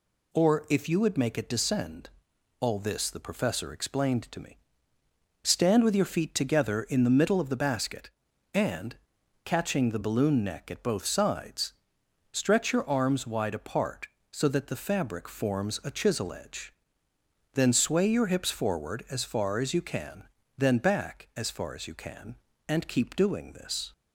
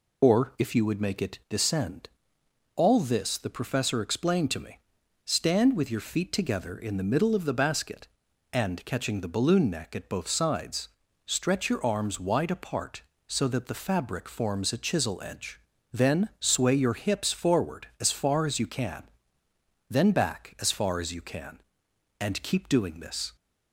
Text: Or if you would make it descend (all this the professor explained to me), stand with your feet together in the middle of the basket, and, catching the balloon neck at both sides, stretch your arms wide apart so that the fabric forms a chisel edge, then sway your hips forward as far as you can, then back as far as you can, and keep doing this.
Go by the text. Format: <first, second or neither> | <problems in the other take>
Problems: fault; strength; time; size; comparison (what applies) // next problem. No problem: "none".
first | loses the start of "Or"; at 0.2 s; 40 ms